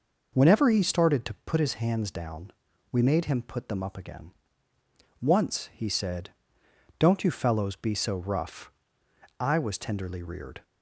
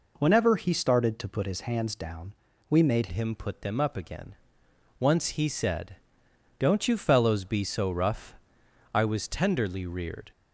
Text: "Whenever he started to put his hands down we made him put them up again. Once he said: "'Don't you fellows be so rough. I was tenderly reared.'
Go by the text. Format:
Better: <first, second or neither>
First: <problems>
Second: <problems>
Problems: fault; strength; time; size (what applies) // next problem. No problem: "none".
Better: first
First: pauses between "down" and "we"; at 2.5 s; 0.38 s long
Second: pauses between "down" and "we"; slight; at 2.3 s; 0.36 s long // changes voice at "him"; from 3.1 s on; 7.2 s long